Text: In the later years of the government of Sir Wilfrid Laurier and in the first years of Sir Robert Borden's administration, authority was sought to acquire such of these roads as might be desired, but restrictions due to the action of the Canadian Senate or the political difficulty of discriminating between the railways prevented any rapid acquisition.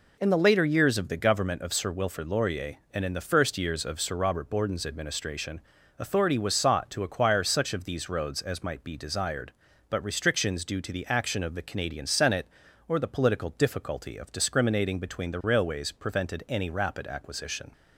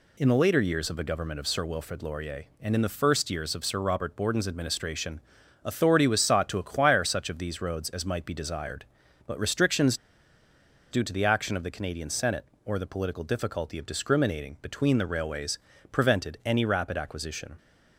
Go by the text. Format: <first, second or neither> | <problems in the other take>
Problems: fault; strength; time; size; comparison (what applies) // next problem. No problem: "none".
first | pauses between "restrictions" and "due"; noticeable; at 9.9 s; 0.95 s long // pauses between "railways" and "prevented"; slight; at 15.5 s; 0.32 s long